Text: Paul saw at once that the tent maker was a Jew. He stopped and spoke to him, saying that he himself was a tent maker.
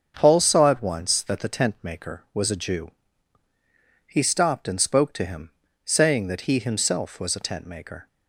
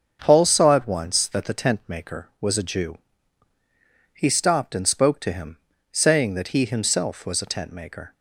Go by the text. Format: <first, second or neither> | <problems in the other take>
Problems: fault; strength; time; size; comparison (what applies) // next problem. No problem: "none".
neither | starts louder than the rest; strong; the same in both